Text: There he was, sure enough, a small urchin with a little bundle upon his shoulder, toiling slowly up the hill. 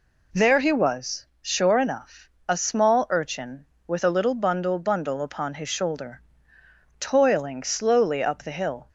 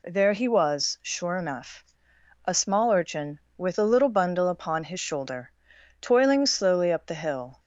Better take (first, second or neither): second